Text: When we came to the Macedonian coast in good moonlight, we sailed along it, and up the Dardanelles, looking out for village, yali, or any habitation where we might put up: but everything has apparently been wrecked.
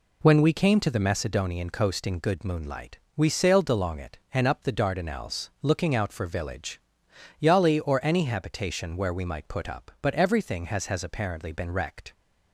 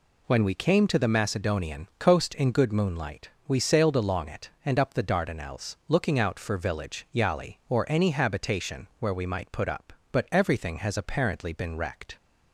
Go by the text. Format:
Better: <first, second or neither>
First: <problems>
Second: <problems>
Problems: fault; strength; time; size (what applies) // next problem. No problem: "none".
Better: second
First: says "has" twice; at 10.8 s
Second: none